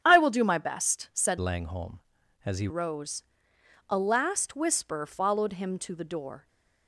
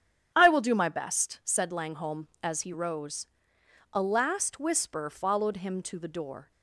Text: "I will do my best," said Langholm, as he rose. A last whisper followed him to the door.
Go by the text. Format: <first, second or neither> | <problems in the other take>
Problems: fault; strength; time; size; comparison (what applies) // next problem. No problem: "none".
second | starts louder than the rest; strong; until 1.0 s; 9.5 dB; strong in the second // changes voice from "Langholm" to "he"; from 1.3 to 2.6 s; 1.3 s long